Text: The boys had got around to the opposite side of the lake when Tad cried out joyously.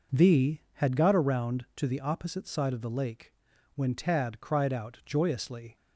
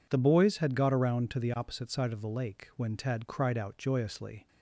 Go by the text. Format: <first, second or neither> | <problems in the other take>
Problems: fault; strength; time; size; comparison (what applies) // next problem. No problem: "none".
second | skips "boys"; at 0.6 s // pauses between "lake" and "when"; at 3.3 s; 0.44 s long